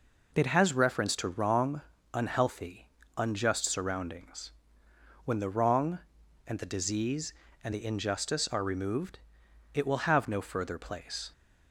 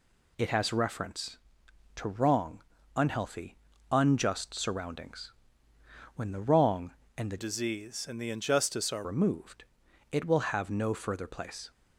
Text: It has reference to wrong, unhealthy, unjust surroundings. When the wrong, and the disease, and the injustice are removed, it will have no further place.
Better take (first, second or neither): first